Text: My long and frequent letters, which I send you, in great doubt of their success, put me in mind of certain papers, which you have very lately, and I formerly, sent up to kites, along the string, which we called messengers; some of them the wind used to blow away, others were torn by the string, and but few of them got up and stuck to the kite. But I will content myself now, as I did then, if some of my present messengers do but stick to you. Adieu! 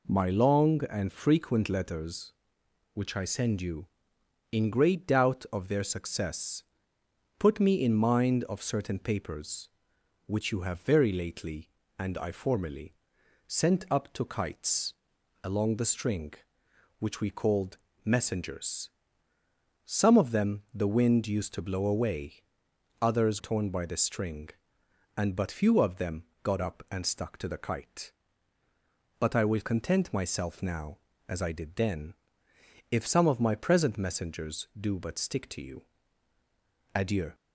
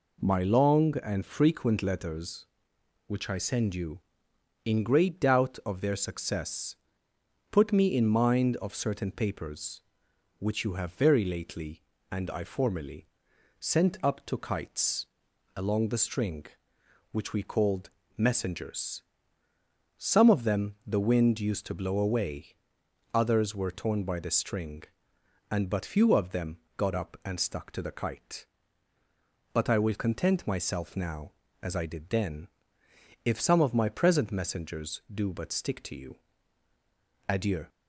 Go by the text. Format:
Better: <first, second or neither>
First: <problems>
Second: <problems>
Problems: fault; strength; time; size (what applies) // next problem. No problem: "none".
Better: second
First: pauses between "called" and "messengers"; slight; at 17.7 s; 0.26 s long // skips "were"; at 23.3 s // pauses between "them" and "got"; slight; at 26.2 s; 0.20 s long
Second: pauses between "called" and "messengers"; slight; at 17.9 s; 0.26 s long // pauses between "them" and "got"; slight; at 26.5 s; 0.20 s long